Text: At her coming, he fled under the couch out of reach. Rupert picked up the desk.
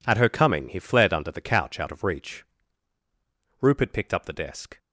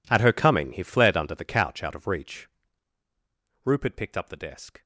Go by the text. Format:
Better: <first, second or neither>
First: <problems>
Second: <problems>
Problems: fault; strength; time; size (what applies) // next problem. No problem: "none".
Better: first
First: none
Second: gets quieter; strong; throughout; 20 dB